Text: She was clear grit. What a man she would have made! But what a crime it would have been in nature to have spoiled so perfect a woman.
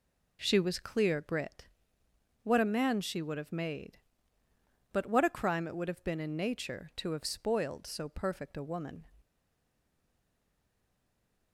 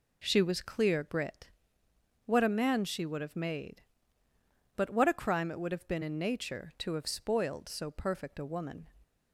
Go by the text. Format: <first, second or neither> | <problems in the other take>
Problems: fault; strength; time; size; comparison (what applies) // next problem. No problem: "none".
second | stays silent after the last word; from 9.2 s on; 2.3 s long